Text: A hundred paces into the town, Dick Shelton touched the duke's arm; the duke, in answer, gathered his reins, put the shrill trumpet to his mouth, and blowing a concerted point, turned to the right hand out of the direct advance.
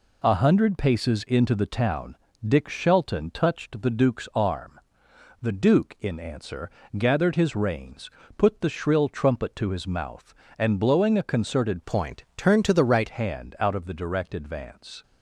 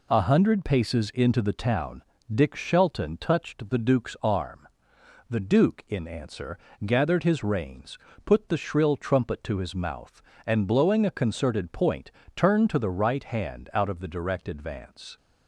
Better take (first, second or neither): second